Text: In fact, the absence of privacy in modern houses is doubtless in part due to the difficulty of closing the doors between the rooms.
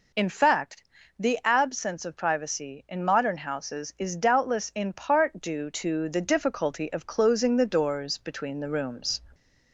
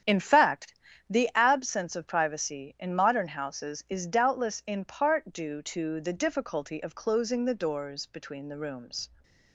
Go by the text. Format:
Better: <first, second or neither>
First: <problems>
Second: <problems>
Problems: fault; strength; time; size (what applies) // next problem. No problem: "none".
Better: first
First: none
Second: gets quieter; strong; throughout; 9.5 dB